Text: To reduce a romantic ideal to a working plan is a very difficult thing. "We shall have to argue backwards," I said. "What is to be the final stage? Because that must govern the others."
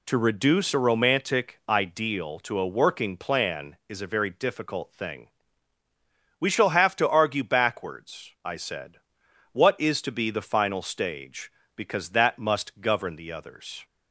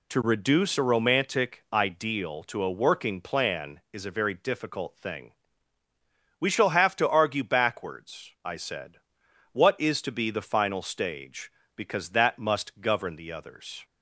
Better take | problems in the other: neither | none

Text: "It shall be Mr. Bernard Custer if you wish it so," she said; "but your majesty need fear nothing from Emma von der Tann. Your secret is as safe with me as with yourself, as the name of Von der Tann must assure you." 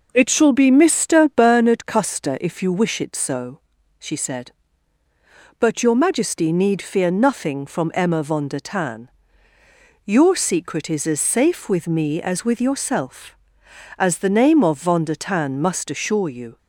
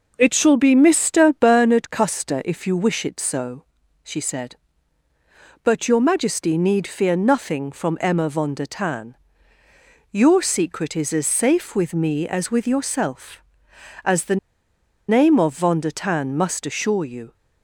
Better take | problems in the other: first | pauses between "the" and "name"; noticeable; at 14.3 s; 0.72 s long

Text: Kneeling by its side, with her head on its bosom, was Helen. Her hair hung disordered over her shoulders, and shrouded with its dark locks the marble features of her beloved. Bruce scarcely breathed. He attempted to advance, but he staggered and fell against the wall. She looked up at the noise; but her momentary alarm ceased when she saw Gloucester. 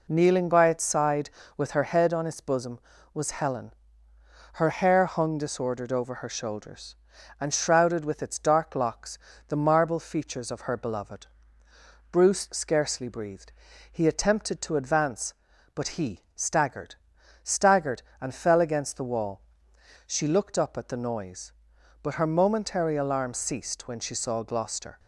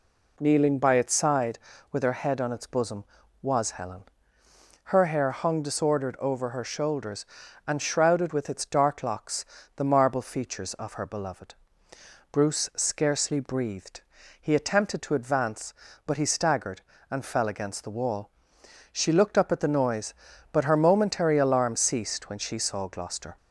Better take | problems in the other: second | pauses between "locks" and "the"; slight; at 9.1 s; 0.32 s long; slight in the second // says "staggered" twice; at 17.4 s

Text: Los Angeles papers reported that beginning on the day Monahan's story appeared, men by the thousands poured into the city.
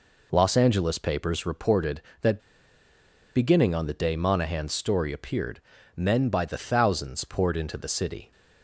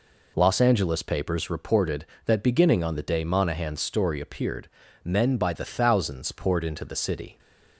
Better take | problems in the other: second | pauses between "that" and "beginning"; noticeable; at 2.3 s; 0.97 s long

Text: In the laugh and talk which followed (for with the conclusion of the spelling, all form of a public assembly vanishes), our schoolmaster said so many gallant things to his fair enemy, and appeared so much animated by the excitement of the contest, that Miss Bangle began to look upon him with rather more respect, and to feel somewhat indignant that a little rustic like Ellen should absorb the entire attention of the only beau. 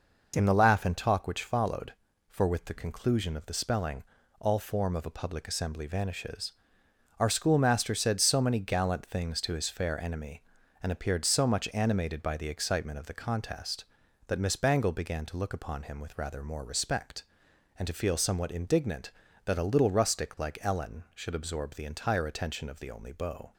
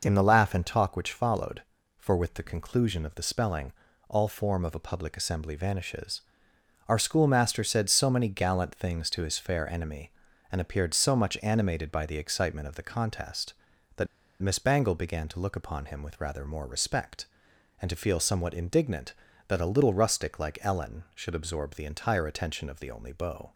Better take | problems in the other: first | pauses between "that" and "Miss"; at 14.0 s; 0.36 s long

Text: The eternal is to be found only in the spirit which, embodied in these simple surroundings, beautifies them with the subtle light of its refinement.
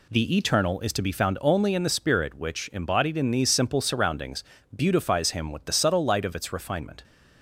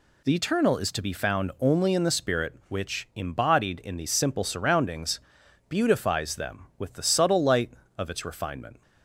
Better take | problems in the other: second | says "him" for "them"; at 5.3 s

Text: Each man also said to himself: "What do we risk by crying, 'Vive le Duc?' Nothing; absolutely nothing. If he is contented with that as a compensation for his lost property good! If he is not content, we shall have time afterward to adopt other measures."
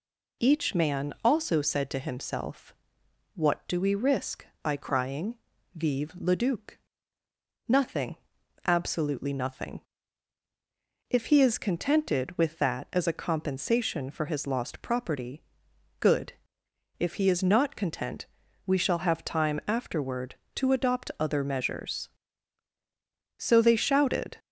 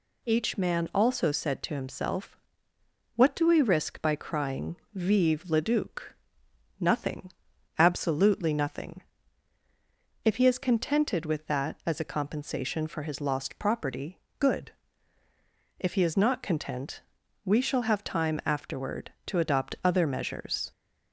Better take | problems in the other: second | pauses between "property" and "good"; noticeable; at 15.4 s; 0.58 s long; slight in the second // goes on to say "So they shouted"; noticeable; from 23.3 s on; 1.0 s long

